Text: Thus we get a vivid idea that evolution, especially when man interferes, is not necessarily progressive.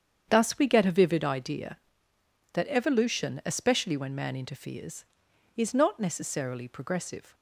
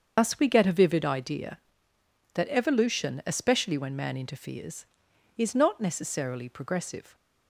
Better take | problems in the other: first | loses the start of "Thus"; at 0.1 s; 70 ms // starts louder than the rest; until 1.1 s; 6.5 dB; strong in the first

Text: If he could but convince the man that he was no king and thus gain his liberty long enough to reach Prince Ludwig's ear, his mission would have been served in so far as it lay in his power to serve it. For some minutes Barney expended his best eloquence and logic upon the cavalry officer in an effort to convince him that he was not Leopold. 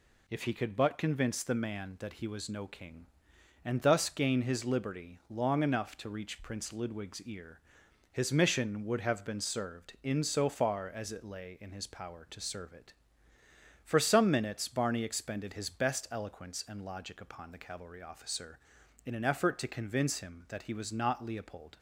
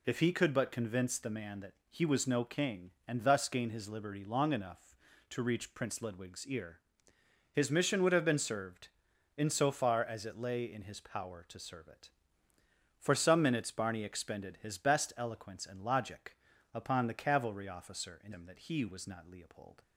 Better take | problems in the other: first | pauses between "that" and "he"; slight; at 1.7 s; 0.16 s long // pauses between "logic" and "upon"; slight; at 16.3 s; 0.34 s long // skips "an effort to convince"; at 18.3 s

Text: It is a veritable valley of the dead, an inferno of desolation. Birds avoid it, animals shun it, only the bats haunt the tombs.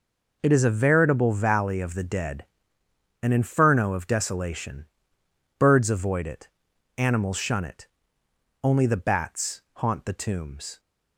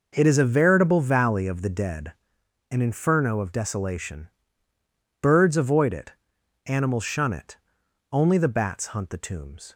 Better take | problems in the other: first | says "hunt" for "haunt"; at 8.8 s

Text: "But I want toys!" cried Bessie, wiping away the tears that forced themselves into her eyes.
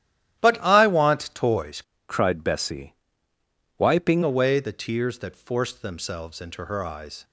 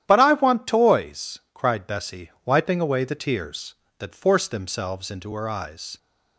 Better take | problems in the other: second | starts louder than the rest; strong; until 1.4 s; 13.5 dB; strong in the second // changes voice from "cried" to "wiping"; from 2.0 to 4.2 s; 2.2 s long

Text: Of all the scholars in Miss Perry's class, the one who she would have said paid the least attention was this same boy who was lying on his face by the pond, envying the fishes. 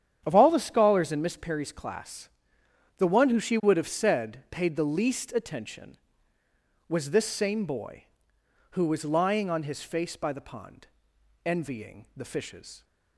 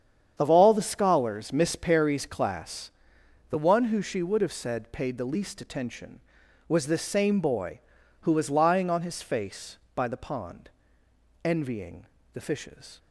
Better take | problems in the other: first | starts louder than the rest; strong; until 1.4 s; 8 dB; strong in the first // skips "in"; at 1.5 s // pauses between "envying" and "the"; slight; at 12.0 s; 0.28 s long

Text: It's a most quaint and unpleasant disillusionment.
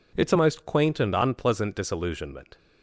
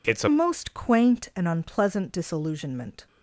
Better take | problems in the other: first | changes voice at "most"; from 0.2 s on; 2.8 s long

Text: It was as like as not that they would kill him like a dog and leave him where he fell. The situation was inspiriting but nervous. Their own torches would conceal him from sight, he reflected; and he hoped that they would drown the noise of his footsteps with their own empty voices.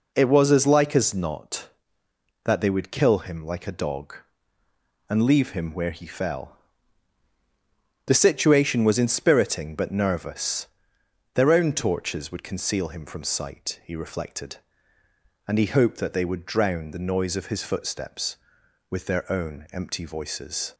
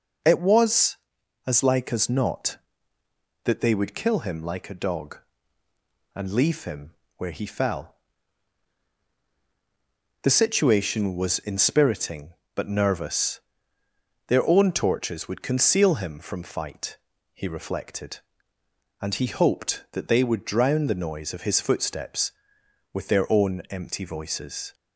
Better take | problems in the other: first | pauses between "him" and "where"; slight; at 6.9 s; 0.24 s long // says "fight" for "sight"; at 16.4 s

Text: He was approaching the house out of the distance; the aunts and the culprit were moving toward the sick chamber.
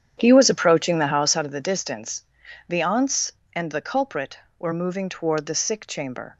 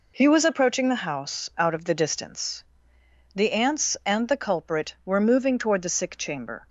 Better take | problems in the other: second | starts louder than the rest; strong; until 1.5 s; 9 dB

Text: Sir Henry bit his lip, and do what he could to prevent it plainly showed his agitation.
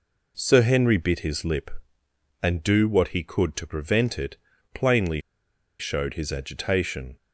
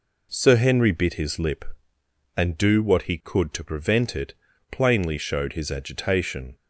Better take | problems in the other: second | pauses between "it" and "plainly"; at 4.3 s; 0.38 s long; also in the second // pauses between "plainly" and "showed"; noticeable; at 5.2 s; 0.58 s long

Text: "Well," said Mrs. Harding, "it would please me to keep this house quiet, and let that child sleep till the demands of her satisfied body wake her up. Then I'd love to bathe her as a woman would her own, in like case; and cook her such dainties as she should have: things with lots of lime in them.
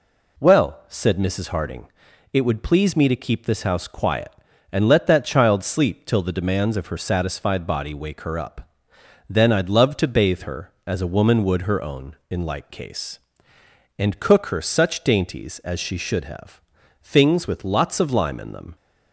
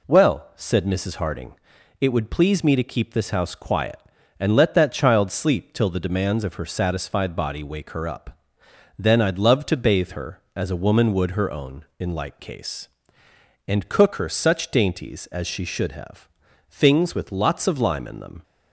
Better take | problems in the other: neither | none

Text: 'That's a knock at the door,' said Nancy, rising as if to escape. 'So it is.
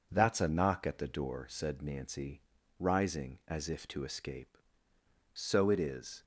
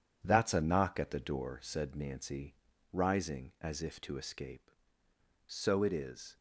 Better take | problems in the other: first | gets quieter; throughout; 6.5 dB

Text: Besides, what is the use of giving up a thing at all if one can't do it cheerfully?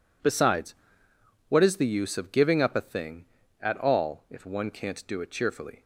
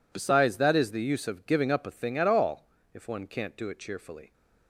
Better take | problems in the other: first | says "that" for "what"; at 0.5 s // pauses between "all" and "if"; slight; at 2.6 s; 0.26 s long

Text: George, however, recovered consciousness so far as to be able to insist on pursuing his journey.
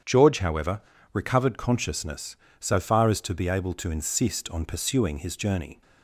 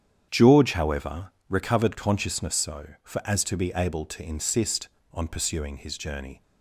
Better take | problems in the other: first | starts louder than the rest; strong; until 1.3 s; 8.5 dB; strong in the first // says "for" for "far"; at 3.0 s

